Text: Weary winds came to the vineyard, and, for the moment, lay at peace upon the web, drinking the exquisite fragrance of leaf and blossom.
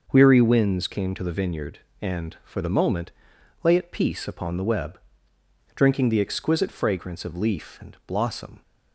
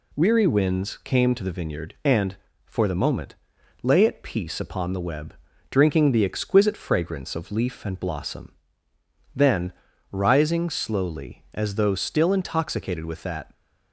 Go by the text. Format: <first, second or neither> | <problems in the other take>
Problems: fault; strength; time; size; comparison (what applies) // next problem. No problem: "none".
first | goes on to say "Then rising slowly as though still intoxicated with that"; strong; from 9.3 s on; 4.1 s long